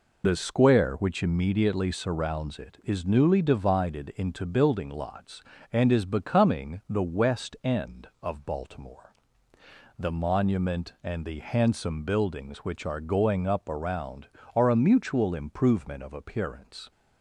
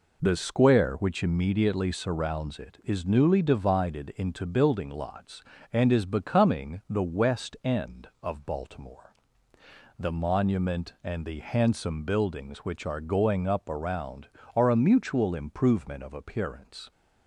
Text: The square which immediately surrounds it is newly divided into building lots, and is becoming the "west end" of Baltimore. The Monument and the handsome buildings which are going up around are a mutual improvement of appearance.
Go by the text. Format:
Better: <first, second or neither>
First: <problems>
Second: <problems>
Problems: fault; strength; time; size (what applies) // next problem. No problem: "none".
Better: second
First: loses the start of "The"; at 0.2 s; 50 ms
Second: none